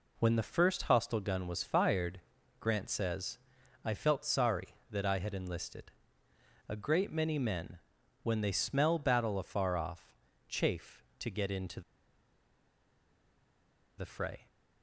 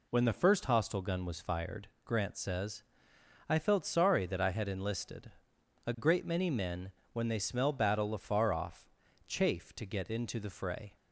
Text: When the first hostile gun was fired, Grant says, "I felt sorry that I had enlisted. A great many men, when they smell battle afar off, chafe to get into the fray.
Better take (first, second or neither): second